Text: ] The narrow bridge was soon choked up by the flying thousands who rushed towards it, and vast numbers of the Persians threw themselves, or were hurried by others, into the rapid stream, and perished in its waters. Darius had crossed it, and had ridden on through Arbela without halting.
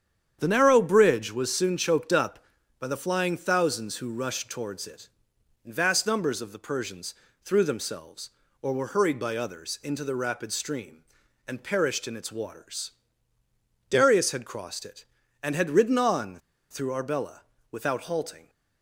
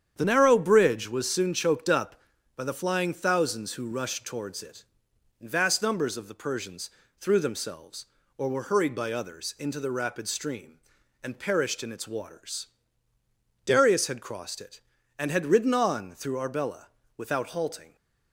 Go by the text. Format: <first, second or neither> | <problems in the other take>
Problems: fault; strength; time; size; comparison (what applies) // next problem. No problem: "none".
second | starts louder than the rest; strong; until 1.4 s; 8.5 dB; strong in the second // pauses between "Persians" and "threw"; slight; at 7.1 s; 0.30 s long; slight in the second // pauses between "on" and "through"; slight; at 16.3 s; 0.32 s long // pauses between "Arbela" and "without"; slight; at 17.3 s; 0.32 s long; slight in the second